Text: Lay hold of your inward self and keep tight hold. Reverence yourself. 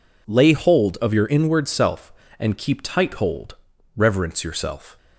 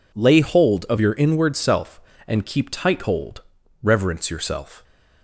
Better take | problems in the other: neither | none

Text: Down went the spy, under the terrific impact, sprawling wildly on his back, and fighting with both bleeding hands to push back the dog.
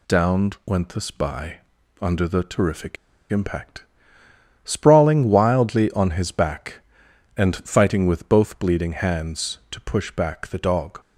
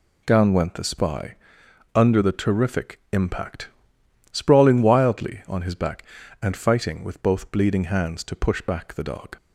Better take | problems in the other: second | pauses between "terrific" and "impact"; slight; at 2.9 s; 0.35 s long

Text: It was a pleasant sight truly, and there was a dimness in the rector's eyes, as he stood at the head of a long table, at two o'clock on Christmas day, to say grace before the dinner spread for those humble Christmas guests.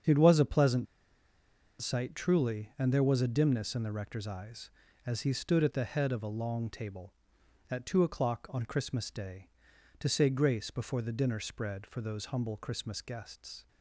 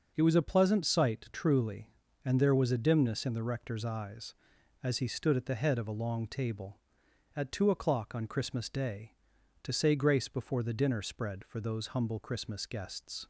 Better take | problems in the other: second | starts louder than the rest; strong; until 2.0 s; 7.5 dB // pauses between "pleasant" and "sight"; noticeable; at 0.8 s; 0.96 s long

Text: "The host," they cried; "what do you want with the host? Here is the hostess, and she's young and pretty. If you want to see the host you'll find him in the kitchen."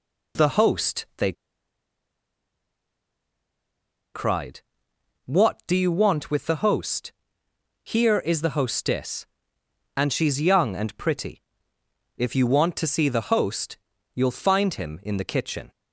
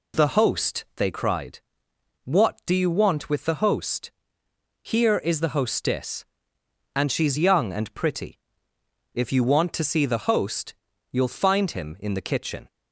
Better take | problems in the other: second | pauses between "they" and "cried"; strong; at 1.3 s; 2.8 s long // pauses between "host" and "you'll"; at 13.7 s; 0.38 s long; also in the second

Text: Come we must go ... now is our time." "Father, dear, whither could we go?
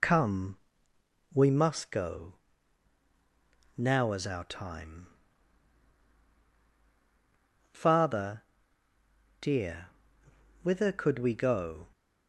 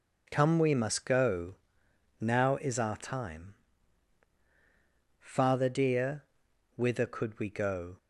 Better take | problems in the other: second | loses the start of "Come"; at 0.0 s; 20 ms // pauses between "Come" and "we"; noticeable; at 0.5 s; 0.74 s long

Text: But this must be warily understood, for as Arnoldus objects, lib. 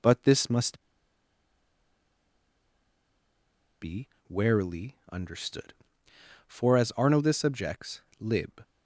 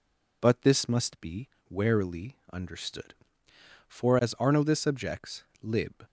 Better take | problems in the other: second | pauses between "must" and "be"; strong; at 0.8 s; 2.9 s long // pauses between "be" and "warily"; slight; at 4.0 s; 0.20 s long; slight in the second // pauses between "warily" and "understood"; slight; at 4.9 s; 0.16 s long; slight in the second

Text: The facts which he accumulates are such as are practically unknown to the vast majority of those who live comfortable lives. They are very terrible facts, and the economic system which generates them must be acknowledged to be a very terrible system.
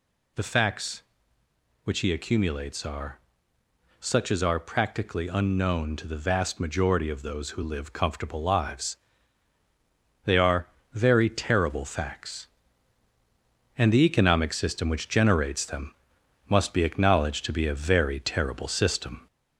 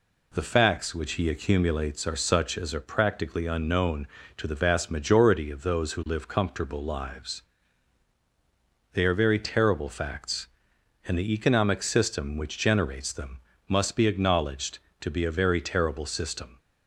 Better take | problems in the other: second | gets louder; slight; throughout; 2 dB // pauses between "are" and "such"; noticeable; at 3.1 s; 0.80 s long // pauses between "are" and "very"; slight; at 10.6 s; 0.24 s long // pauses between "them" and "must"; noticeable; at 15.9 s; 0.56 s long; slight in the second

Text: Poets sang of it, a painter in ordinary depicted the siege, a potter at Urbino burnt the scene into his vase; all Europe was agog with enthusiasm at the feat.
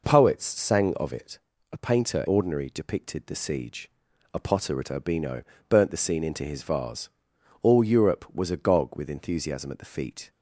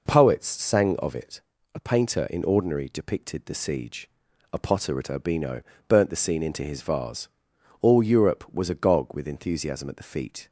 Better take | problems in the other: second | skips "in"; at 2.2 s // pauses between "Urbino" and "burnt"; slight; at 5.4 s; 0.26 s long; slight in the second

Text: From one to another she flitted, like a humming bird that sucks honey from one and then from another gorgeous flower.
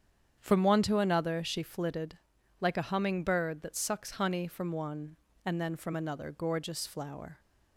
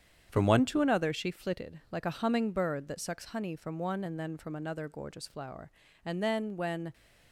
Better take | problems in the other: first | starts louder than the rest; strong; until 1.3 s; 8.5 dB; strong in the first // goes on to say "And then when"; noticeable; from 6.0 s on; 0.88 s long

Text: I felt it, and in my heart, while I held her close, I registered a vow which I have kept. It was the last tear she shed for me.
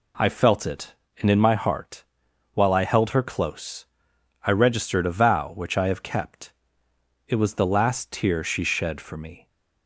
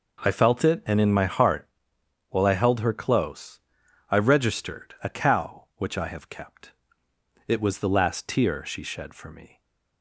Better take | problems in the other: first | says "cow" for "vow"; at 5.0 s

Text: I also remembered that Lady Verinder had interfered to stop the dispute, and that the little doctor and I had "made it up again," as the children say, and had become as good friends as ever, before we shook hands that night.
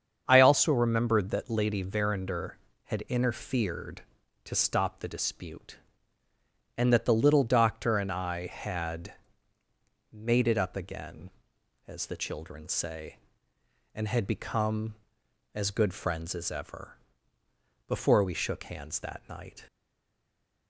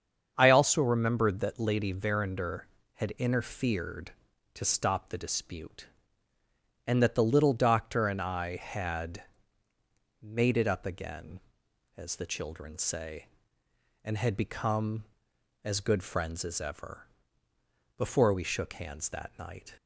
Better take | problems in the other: second | starts louder than the rest; strong; until 1.2 s; 7.5 dB; strong in the second // pauses between "had" and "made"; noticeable; at 9.1 s; 0.98 s long; noticeable in the second // stays silent after the last word; from 19.6 s on; 1.0 s long

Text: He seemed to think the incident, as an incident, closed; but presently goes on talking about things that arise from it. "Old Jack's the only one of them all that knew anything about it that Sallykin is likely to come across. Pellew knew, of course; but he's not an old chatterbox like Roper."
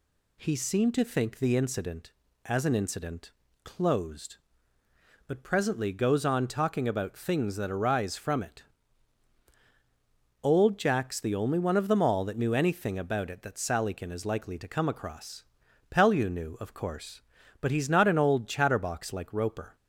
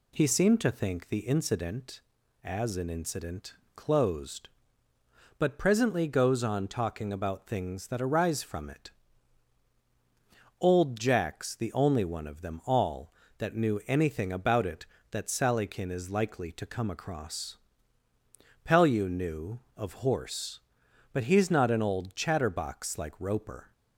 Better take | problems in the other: first | says "horse" for "course"; at 19.9 s

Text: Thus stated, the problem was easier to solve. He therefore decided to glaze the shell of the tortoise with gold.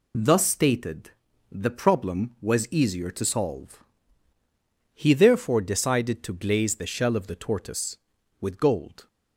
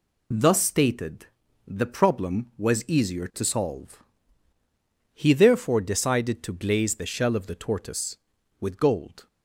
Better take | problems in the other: neither | none

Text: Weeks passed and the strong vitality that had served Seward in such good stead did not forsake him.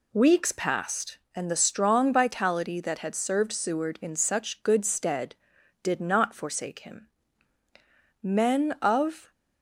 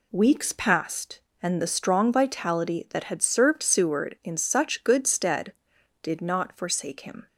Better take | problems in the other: second | goes on to say "Men of"; noticeable; from 8.2 s on; 1.0 s long

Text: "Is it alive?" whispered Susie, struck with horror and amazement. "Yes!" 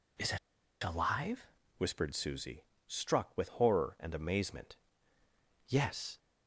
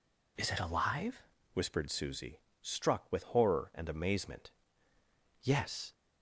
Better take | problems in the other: second | pauses between "it" and "alive"; at 0.3 s; 0.45 s long

